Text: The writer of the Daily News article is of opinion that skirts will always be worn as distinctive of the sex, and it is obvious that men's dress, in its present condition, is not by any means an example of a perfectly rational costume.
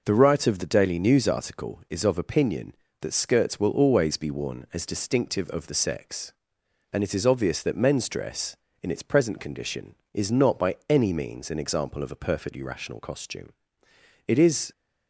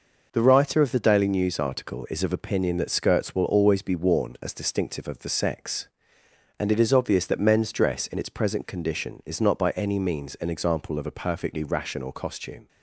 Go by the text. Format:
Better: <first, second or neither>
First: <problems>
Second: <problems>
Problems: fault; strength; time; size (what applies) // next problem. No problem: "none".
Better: second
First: goes on to say "It is"; slight; from 14.2 s on; 0.46 s long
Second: none